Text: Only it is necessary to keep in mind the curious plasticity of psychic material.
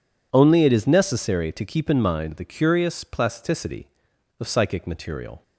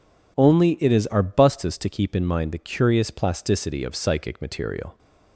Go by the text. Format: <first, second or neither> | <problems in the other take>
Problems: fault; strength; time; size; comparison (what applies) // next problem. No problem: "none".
first | says "arbustus" for "necessary"; at 1.1 s